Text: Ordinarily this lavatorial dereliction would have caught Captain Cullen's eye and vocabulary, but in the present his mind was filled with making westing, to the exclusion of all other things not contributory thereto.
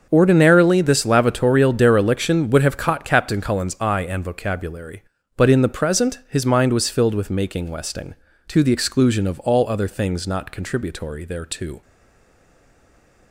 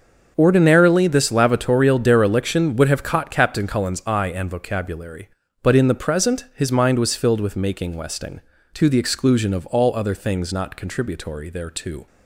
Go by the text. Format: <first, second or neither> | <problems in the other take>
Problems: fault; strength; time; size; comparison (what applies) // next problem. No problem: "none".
second | starts louder than the rest; noticeable; until 1.1 s; 6 dB; noticeable in the second // stays silent after the last word; noticeable; from 11.8 s on; 1.5 s long